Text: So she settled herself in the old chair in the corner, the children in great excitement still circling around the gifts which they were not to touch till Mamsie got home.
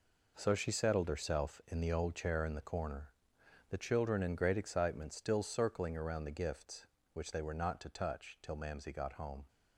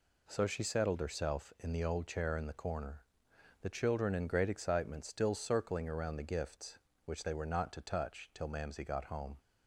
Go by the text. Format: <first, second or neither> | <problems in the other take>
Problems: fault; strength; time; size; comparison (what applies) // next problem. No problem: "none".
second | gets quieter; strong; throughout; 9.5 dB